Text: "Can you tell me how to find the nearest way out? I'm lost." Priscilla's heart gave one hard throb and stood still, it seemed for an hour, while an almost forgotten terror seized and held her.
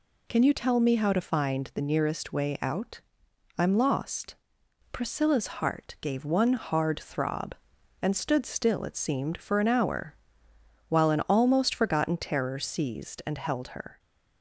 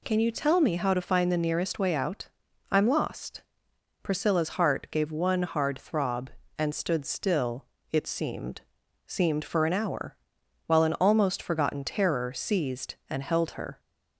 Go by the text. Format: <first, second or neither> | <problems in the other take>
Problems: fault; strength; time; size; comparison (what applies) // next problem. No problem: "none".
first | says "seemed" twice; at 9.0 s